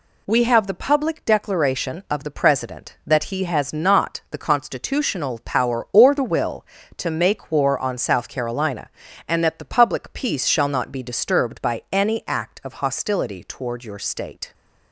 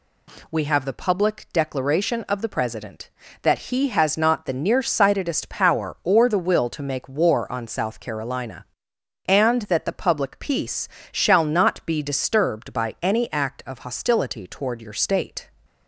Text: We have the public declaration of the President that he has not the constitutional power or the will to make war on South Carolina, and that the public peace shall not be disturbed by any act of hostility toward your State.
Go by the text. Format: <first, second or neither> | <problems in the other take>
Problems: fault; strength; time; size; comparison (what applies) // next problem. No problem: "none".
first | says "nearsightedest" for "constitutional"; at 4.5 s // pauses between "peace" and "shall"; slight; at 10.8 s; 0.24 s long